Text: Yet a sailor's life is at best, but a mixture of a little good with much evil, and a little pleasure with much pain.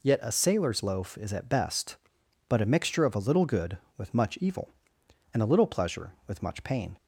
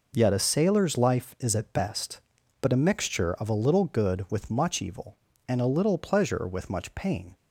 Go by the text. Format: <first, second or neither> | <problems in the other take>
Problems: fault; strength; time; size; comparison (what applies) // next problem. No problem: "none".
second | says "loaf" for "life"; at 0.8 s